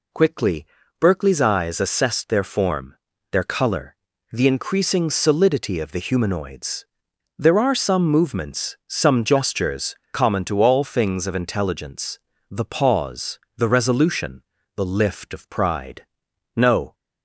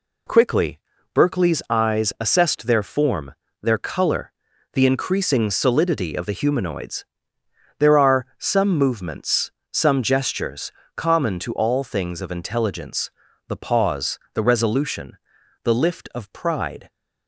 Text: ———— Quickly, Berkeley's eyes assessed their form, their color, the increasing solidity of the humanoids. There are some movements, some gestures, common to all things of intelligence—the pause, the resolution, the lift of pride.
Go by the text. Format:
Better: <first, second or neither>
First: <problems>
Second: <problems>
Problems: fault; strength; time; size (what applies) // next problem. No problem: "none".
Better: second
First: goes on to say "No"; slight; from 16.5 s on; 0.38 s long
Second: none